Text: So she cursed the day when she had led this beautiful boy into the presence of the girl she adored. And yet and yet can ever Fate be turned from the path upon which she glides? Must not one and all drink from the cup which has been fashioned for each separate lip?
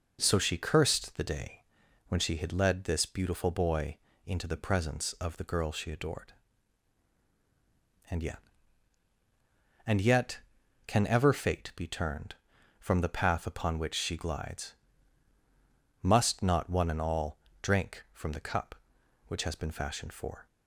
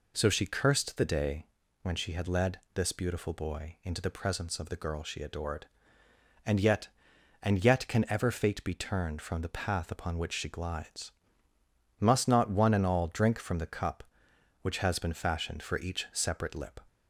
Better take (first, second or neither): second